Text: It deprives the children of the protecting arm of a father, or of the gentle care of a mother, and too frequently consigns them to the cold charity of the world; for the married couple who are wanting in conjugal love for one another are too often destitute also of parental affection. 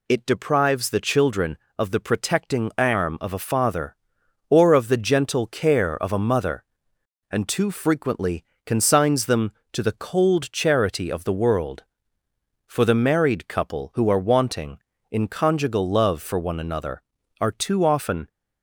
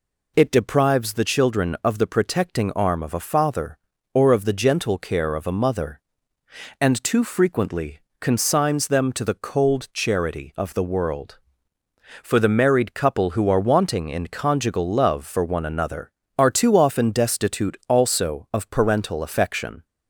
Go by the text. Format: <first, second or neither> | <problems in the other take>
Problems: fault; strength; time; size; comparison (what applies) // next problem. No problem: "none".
second | pauses between "frequently" and "consigns"; slight; at 8.4 s; 0.22 s long; slight in the second // stops before "destitute also of parental affection"; at 18.2 s